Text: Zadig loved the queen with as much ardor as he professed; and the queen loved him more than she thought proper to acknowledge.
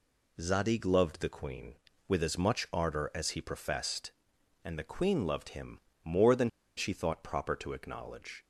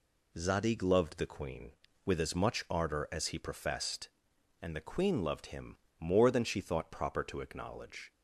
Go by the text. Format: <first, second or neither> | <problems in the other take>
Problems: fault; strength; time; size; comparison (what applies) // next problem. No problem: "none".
second | pauses between "him" and "more"; slight; at 5.8 s; 0.22 s long; slight in the second // pauses between "than" and "she"; slight; at 6.4 s; 0.28 s long